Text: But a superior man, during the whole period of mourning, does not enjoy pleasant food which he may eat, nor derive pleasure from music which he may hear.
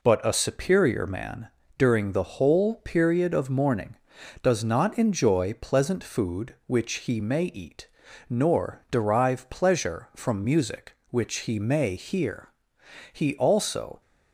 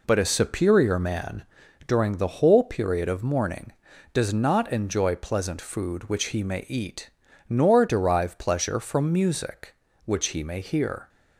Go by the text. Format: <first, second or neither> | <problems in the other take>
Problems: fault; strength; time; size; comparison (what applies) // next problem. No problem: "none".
second | goes on to say "He also"; noticeable; from 13.1 s on; 0.88 s long